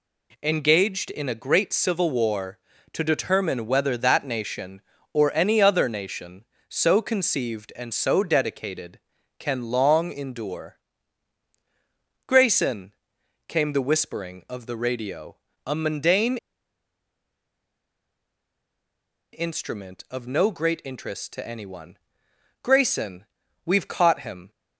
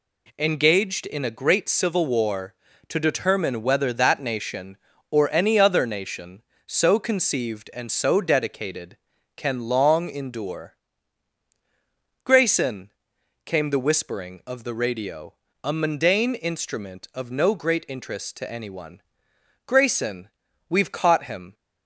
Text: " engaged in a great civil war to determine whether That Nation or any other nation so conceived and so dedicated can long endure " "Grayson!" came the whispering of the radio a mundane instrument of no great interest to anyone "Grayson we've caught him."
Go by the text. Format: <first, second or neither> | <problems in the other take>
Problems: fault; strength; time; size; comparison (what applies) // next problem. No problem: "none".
second | pauses between "radio" and "a"; slight; at 15.3 s; 0.26 s long; slight in the second // pauses between "mundane" and "instrument"; strong; at 16.3 s; 2.9 s long // pauses between "anyone" and "Grayson"; noticeable; at 21.9 s; 0.68 s long; noticeable in the second // pauses between "Grayson" and "we've"; at 23.2 s; 0.40 s long; also in the second